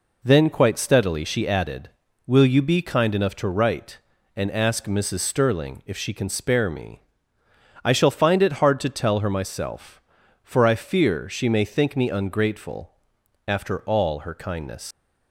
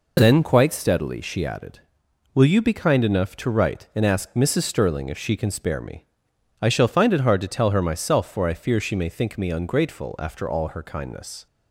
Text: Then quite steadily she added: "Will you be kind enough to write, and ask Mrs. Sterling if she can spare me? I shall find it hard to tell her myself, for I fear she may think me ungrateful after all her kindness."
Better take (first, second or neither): second